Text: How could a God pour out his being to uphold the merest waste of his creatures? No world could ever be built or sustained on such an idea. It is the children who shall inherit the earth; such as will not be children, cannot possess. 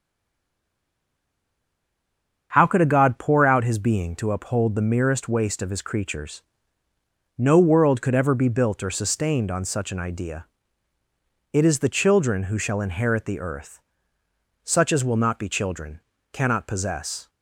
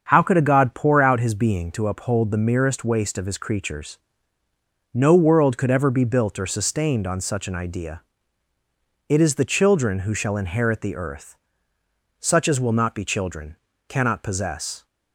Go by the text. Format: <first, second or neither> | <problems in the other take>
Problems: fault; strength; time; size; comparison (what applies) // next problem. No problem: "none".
second | stays silent before the first word; until 2.5 s; 2.5 s long // starts louder than the rest; strong; until 3.5 s; 7 dB; also in the second